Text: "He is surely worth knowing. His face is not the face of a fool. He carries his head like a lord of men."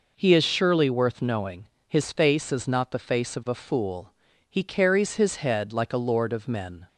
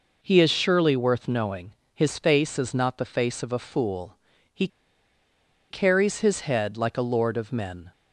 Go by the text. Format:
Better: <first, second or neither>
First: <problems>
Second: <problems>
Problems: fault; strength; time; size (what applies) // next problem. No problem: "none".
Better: first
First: none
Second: pauses between "He" and "carries"; at 4.6 s; 1.0 s long